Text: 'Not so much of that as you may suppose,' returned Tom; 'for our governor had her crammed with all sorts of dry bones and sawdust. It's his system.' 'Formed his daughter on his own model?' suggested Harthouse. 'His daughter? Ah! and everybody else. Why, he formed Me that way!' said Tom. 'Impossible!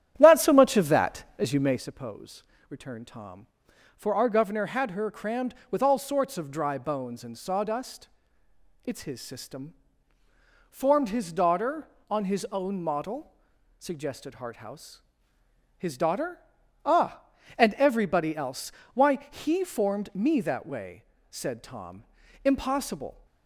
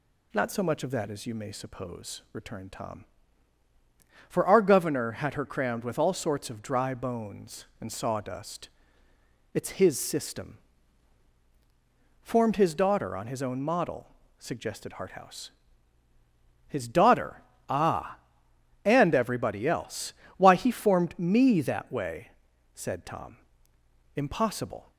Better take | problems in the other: second | starts louder than the rest; strong; until 1.8 s; 10 dB

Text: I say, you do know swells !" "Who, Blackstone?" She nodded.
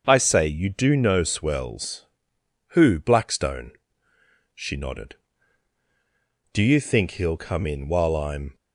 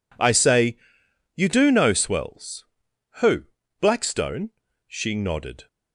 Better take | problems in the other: second | starts louder than the rest; until 1.0 s; 6.5 dB // goes on to say "Do you think he'll come in while I'm"; strong; from 6.5 s on; 2.0 s long

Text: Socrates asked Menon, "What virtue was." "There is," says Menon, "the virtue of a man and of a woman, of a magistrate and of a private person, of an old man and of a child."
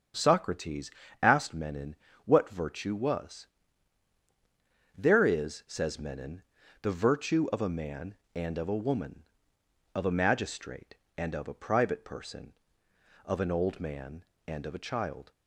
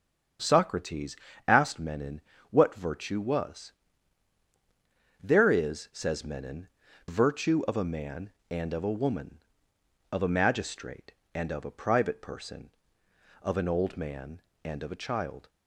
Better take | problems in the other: first | starts louder than the rest; strong; until 1.7 s; 7 dB; strong in the first // pauses between "Socrates" and "asked"; slight; at 1.1 s; 0.30 s long; slight in the first // skips "the"; at 6.8 s

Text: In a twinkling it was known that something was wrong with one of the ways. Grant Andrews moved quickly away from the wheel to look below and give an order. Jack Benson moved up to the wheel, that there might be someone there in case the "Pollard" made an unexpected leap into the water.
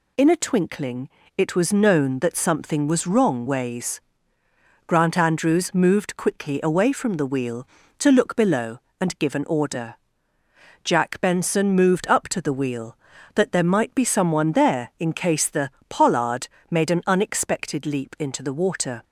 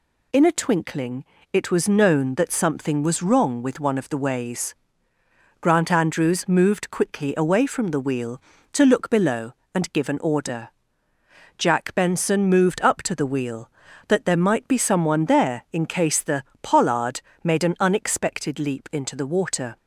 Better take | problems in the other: second | pauses between "twinkling" and "it"; slight; at 1.0 s; 0.30 s long; slight in the second // skips "with one of the"; at 3.4 s // pauses between "the" and "Pollard"; slight; at 15.6 s; 0.18 s long; slight in the second // pauses between "Pollard" and "made"; slight; at 16.4 s; 0.24 s long; slight in the second

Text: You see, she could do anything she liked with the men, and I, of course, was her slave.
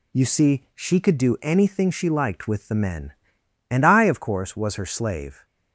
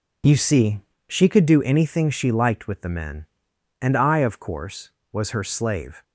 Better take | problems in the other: neither | none

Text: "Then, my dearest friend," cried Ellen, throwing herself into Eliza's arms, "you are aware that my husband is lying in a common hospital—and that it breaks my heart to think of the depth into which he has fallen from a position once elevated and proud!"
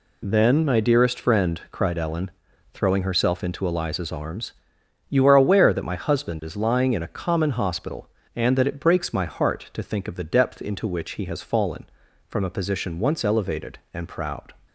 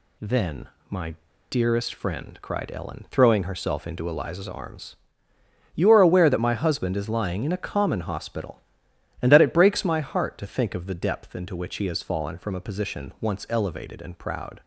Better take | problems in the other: first | pauses between "my" and "dearest"; slight; at 1.1 s; 0.35 s long

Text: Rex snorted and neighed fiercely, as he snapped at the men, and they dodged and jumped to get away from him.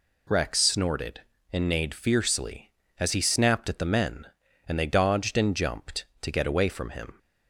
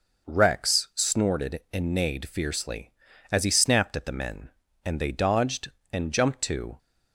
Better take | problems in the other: first | stops before "get away from him"; at 6.7 s

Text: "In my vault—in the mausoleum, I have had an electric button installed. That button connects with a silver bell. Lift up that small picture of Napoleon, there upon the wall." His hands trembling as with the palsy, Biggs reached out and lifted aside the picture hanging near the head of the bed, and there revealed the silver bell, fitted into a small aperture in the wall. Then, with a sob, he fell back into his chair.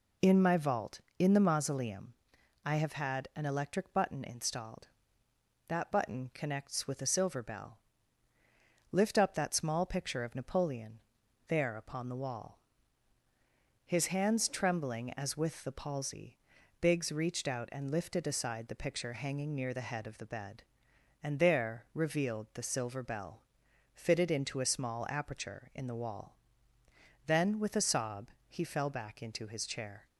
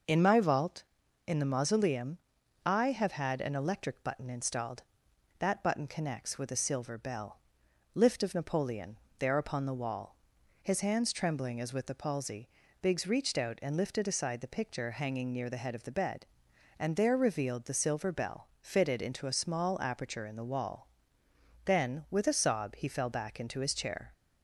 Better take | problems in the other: first | skips "up that small picture"; at 8.2 s

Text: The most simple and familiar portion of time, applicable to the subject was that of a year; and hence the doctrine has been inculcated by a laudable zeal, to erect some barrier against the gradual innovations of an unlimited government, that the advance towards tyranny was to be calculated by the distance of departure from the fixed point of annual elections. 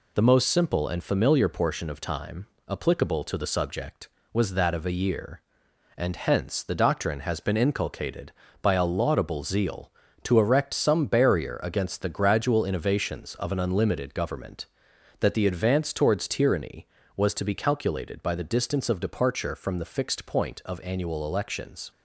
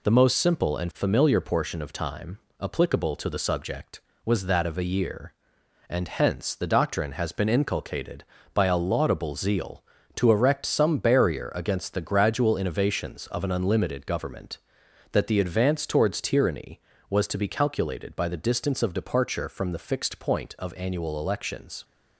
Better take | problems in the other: neither | none

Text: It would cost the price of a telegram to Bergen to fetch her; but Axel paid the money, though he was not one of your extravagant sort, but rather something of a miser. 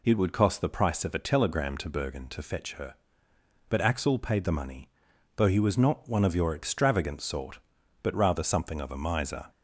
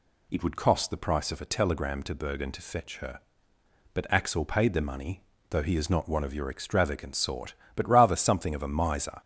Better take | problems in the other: first | says "is" for "was"; at 5.7 s

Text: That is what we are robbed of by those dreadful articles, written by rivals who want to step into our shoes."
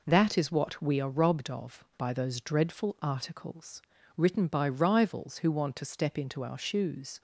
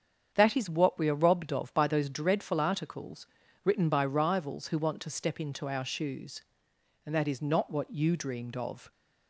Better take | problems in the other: first | starts louder than the rest; strong; until 1.3 s; 8 dB // goes on to say "And that is not what you dreamed of"; strong; from 7.0 s on; 1.8 s long

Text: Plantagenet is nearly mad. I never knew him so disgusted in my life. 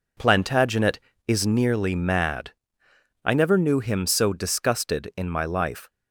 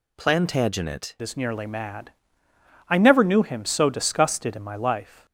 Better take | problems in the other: first | changes voice at "is"; from 1.2 s on; 4.0 s long

